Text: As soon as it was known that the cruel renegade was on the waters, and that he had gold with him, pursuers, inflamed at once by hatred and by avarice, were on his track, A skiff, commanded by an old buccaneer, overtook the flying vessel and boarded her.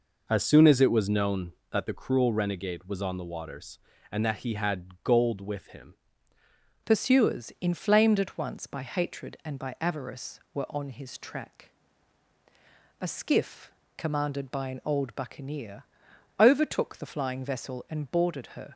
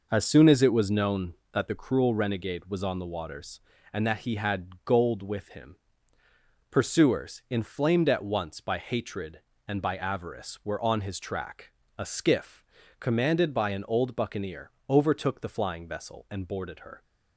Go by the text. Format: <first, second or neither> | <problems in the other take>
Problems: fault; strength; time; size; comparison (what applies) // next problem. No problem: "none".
second | changes voice at "pursuers"; from 6.8 s on; 11.9 s long